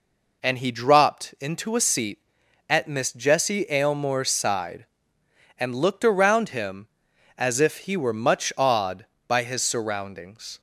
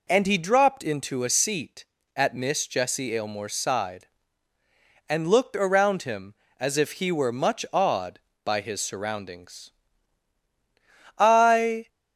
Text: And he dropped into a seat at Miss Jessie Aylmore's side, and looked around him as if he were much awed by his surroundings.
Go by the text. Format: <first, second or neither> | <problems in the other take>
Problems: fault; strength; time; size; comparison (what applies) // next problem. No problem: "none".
first | goes on to say "I"; noticeable; from 11.1 s on; 0.70 s long